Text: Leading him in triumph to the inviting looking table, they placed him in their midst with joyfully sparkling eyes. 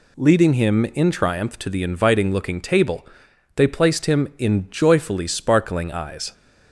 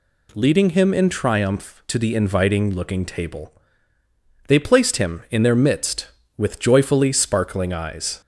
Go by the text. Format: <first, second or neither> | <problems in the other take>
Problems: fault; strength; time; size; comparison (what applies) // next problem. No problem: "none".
second | skips "their midst with"; at 4.6 s